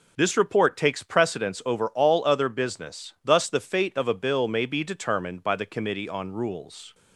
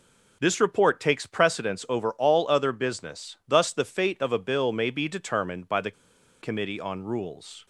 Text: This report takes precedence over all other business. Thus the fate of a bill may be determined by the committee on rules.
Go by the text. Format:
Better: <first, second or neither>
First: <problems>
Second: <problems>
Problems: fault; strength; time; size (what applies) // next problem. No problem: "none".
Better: first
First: none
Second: pauses between "the" and "committee"; noticeable; at 5.9 s; 0.49 s long